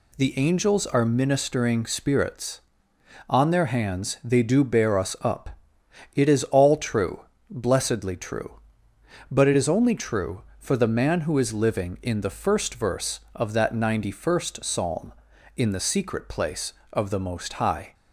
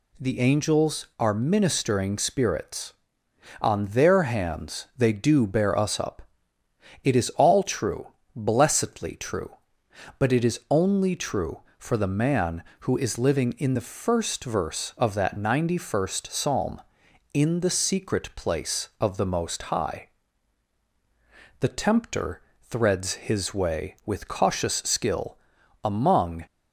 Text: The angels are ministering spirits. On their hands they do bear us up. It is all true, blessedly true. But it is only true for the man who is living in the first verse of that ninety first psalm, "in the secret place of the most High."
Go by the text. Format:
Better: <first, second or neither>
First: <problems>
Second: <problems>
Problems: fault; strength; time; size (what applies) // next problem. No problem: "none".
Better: first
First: none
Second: goes on to say "The tempter threads his way with cautious skill among"; strong; from 21.6 s on; 4.8 s long